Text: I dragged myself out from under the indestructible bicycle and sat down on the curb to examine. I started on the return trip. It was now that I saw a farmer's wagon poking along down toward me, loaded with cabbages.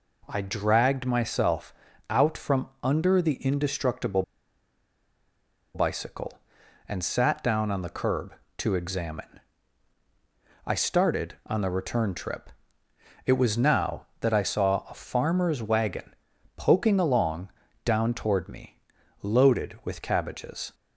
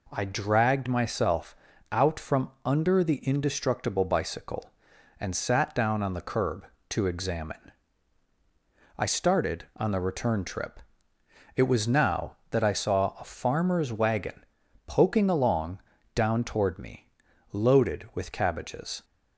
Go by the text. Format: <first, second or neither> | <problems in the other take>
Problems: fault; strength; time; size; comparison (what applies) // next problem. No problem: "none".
second | pauses between "myself" and "out"; slight; at 1.7 s; 0.34 s long; slight in the second // pauses between "indestructible" and "bicycle"; strong; at 4.2 s; 1.5 s long // pauses between "wagon" and "poking"; at 16.1 s; 0.42 s long; also in the second // pauses between "along" and "down"; slight; at 17.4 s; 0.36 s long; slight in the second